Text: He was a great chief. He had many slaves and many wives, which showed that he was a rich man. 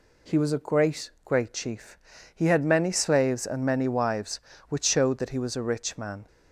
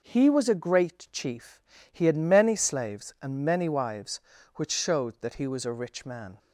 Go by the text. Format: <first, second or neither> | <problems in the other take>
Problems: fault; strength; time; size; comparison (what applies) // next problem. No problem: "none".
second | says "great" twice; at 1.2 s